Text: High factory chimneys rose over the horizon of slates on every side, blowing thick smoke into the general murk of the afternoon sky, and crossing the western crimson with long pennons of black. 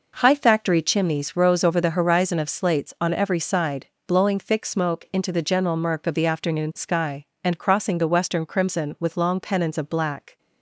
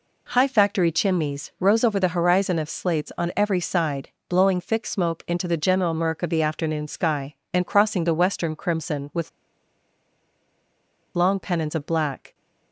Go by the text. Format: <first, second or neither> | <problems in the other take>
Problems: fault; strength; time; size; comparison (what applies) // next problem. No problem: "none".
first | pauses between "with" and "long"; strong; at 9.2 s; 1.8 s long